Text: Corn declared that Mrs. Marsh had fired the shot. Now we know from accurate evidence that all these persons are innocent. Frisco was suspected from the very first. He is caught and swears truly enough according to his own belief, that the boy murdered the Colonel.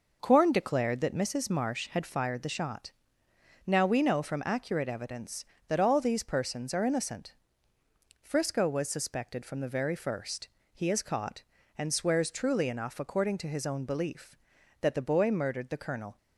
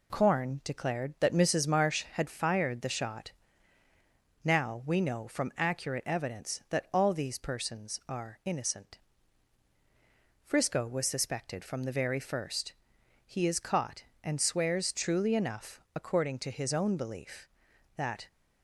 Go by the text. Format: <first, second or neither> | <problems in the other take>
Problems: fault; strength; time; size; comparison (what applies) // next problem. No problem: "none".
first | pauses between "enough" and "according"; slight; at 15.7 s; 0.16 s long // stops before "the boy murdered the Colonel"; at 18.2 s